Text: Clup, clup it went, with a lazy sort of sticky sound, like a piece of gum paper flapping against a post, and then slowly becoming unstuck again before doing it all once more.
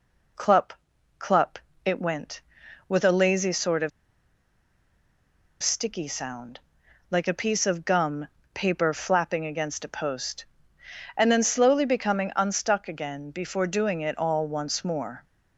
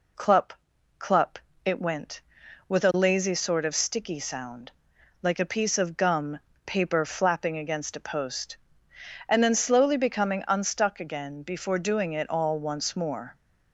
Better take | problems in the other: second | pauses between "clup" and "it"; slight; at 1.5 s; 0.26 s long; slight in the second // pauses between "of" and "sticky"; strong; at 3.9 s; 1.7 s long // pauses between "gum" and "paper"; slight; at 8.2 s; 0.26 s long; slight in the second

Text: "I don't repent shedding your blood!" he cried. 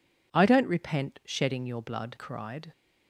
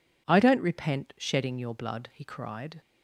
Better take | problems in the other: second | skips "he"; at 2.1 s

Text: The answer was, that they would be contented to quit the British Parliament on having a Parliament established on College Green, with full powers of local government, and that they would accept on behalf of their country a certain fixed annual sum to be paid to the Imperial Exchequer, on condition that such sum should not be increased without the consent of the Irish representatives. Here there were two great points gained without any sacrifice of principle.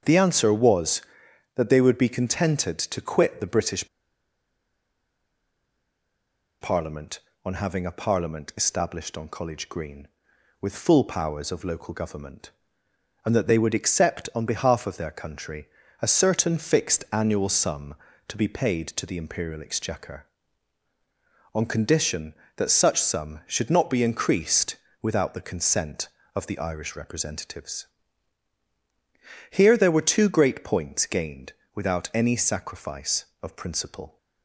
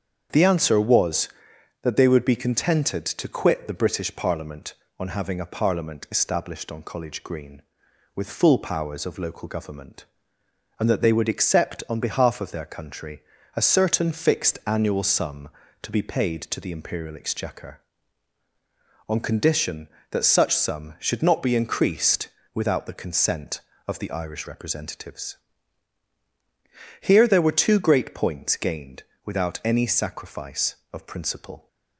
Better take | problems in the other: second | starts louder than the rest; strong; until 1.5 s; 7 dB; strong in the second // pauses between "British" and "Parliament"; strong; at 3.8 s; 2.7 s long // pauses between "country" and "a"; slight; at 15.6 s; 0.34 s long; slight in the second // pauses between "increased" and "without"; slight; at 24.7 s; 0.26 s long; slight in the second // pauses between "gained" and "without"; slight; at 31.5 s; 0.24 s long; slight in the second

